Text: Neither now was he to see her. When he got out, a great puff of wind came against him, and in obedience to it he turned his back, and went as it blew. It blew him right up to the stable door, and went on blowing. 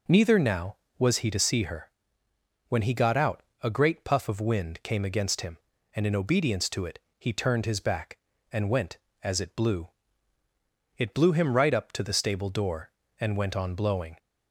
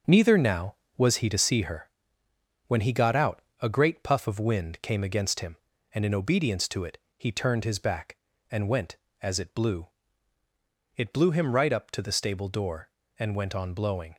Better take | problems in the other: first | gets quieter; throughout; 6.5 dB // pauses between "it" and "he"; slight; at 6.9 s; 0.20 s long; slight in the first

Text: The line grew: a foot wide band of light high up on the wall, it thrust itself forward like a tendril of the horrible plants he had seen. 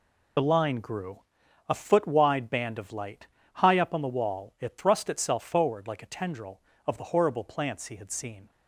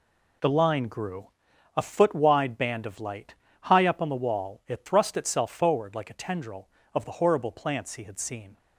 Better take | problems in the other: second | loses the start of "The"; at 0.3 s; 25 ms // pauses between "light" and "high"; slight; at 3.2 s; 0.26 s long; slight in the second

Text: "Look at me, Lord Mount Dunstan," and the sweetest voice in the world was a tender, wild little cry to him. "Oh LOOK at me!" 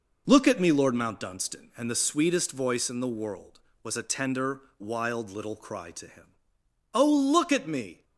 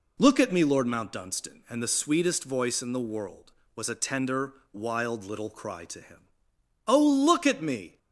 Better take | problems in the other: second | gets quieter; throughout; 6.5 dB

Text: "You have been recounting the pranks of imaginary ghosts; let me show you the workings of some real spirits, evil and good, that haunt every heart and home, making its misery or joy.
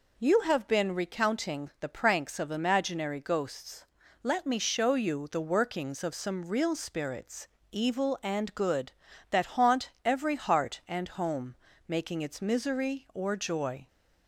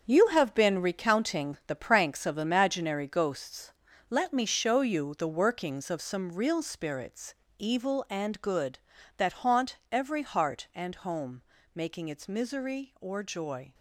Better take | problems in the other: first | gets quieter; strong; throughout; 10 dB // pauses between "haunt" and "every"; slight; at 9.7 s; 0.16 s long; slight in the first

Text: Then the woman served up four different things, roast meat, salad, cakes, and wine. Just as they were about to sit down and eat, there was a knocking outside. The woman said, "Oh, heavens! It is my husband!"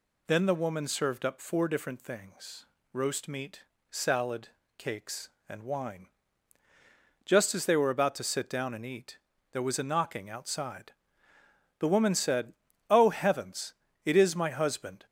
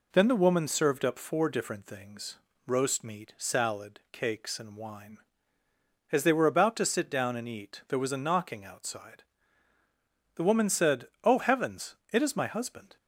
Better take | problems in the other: first | skips "Just"; at 5.6 s

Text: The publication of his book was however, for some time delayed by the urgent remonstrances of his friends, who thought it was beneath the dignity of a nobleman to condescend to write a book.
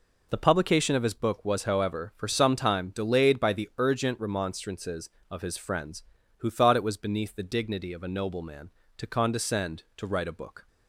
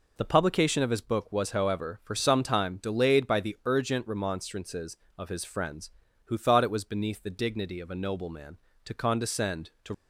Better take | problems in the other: first | stops before "write a book"; at 9.9 s

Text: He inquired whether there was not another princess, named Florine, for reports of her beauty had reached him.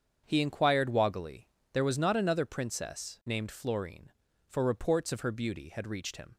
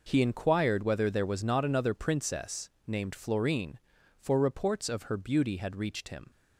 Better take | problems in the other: second | starts louder than the rest; strong; until 1.2 s; 7.5 dB // says "woggily" for "whether"; at 0.8 s

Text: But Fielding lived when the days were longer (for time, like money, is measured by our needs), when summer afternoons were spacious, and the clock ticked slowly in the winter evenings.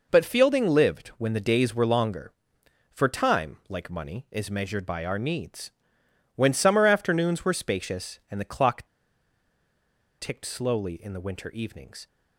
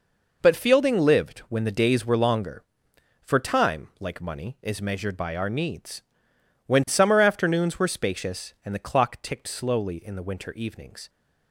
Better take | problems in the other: second | pauses between "clock" and "ticked"; strong; at 8.8 s; 1.3 s long

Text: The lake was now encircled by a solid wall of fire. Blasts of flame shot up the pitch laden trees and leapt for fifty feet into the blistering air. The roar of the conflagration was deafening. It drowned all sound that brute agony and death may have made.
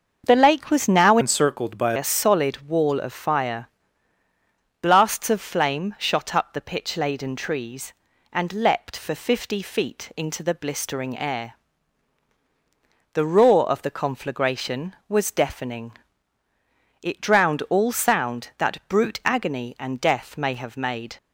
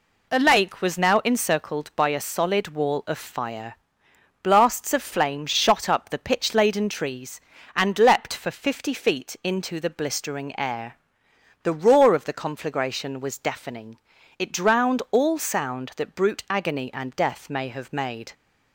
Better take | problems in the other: second | starts louder than the rest; until 1.2 s; 6.5 dB // changes voice from "encircled" to "by"; from 1.2 to 1.9 s; 0.7 s long

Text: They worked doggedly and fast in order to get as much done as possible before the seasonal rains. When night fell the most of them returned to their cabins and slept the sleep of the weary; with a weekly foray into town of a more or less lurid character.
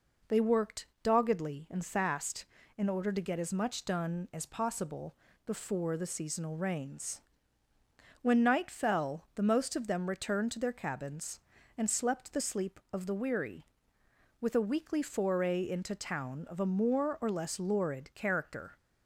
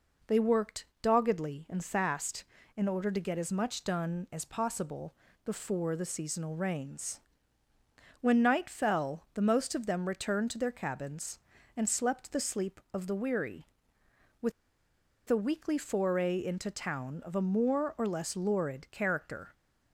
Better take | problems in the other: first | pauses between "worked" and "doggedly"; slight; at 0.8 s; 0.16 s long; slight in the first // pauses between "possible" and "before"; slight; at 5.1 s; 0.30 s long; slight in the first // pauses between "with" and "a"; noticeable; at 14.5 s; 0.77 s long

